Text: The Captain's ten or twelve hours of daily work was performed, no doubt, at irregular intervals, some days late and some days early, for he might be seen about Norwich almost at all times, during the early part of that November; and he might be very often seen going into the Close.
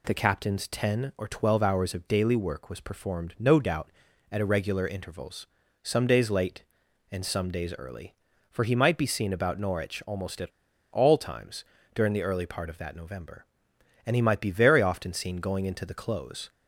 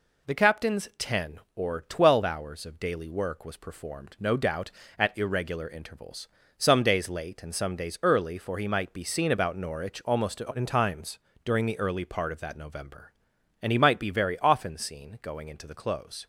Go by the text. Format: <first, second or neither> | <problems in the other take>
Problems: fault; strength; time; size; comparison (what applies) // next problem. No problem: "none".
second | pauses between "at" and "all"; at 10.4 s; 0.42 s long